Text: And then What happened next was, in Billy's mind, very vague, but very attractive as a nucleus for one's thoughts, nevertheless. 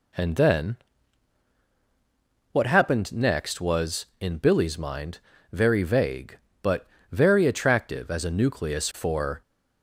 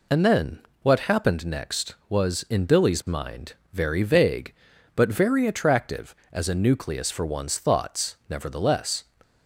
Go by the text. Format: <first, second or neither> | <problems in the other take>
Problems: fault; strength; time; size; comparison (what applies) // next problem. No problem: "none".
second | pauses between "then" and "What"; strong; at 0.7 s; 1.7 s long; slight in the second // pauses between "but" and "very"; slight; at 6.8 s; 0.26 s long // stops before "one's thoughts nevertheless"; at 9.4 s